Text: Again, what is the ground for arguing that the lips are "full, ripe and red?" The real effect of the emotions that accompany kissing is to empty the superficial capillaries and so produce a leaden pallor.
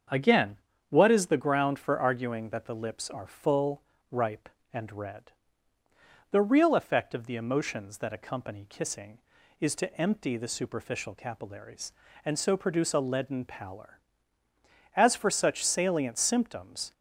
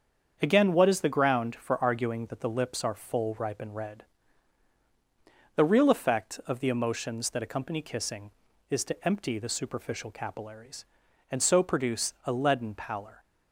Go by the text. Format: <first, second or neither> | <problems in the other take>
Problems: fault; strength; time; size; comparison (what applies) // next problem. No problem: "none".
second | starts louder than the rest; until 1.4 s; 7 dB; strong in the second // goes on to say "As for such salient symptoms"; strong; from 14.9 s on; 1.9 s long